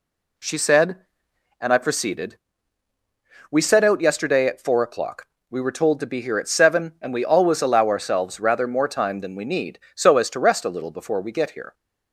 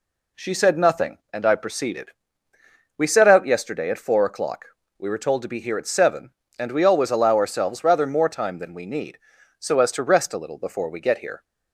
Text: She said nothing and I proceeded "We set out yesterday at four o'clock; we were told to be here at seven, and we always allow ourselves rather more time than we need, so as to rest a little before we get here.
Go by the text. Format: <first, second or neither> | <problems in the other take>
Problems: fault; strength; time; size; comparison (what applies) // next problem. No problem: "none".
second | skips "nothing"; at 1.3 s // pauses between "proceeded" and "We"; at 2.3 s; 1.1 s long; noticeable in the second